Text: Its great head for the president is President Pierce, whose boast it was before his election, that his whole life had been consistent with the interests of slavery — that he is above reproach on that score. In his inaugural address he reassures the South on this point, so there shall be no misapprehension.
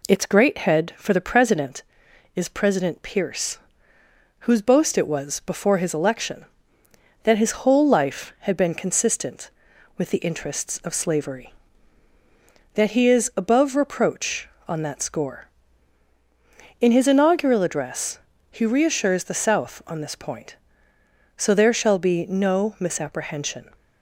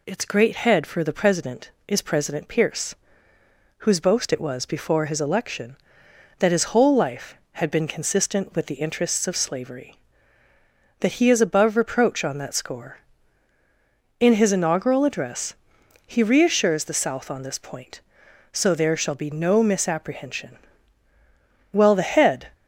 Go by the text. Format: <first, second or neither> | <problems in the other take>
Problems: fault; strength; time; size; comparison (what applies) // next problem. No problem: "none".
first | pauses between "address" and "he"; noticeable; at 15.5 s; 0.50 s long; slight in the first // goes on to say "Well the head"; noticeable; from 21.7 s on; 0.76 s long